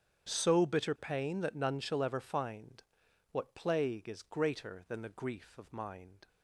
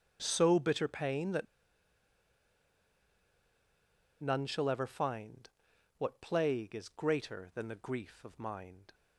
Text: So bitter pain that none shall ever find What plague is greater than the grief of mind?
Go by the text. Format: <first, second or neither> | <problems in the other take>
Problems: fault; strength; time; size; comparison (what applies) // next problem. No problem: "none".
first | starts louder than the rest; strong; until 1.2 s; 8 dB; strong in the first // pauses between "that" and "none"; strong; at 1.4 s; 2.7 s long // pauses between "find" and "What"; noticeable; at 5.4 s; 0.48 s long; noticeable in the first